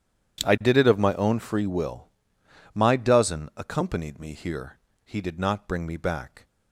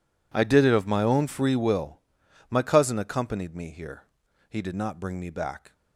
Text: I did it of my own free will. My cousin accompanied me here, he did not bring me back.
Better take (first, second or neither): second